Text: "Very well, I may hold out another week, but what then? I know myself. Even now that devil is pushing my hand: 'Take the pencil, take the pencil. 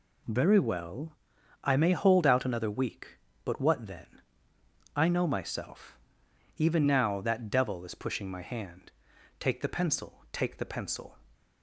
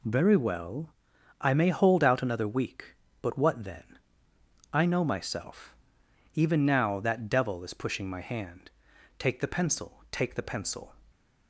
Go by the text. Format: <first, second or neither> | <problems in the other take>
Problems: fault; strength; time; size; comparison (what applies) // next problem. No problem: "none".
neither | none